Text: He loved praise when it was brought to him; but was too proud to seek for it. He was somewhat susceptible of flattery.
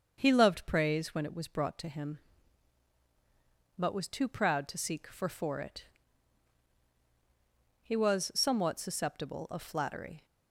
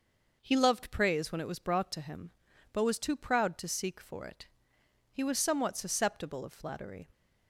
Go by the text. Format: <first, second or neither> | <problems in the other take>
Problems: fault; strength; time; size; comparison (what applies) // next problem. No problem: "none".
second | starts louder than the rest; until 1.1 s; 6.5 dB // says "for" twice; at 5.2 s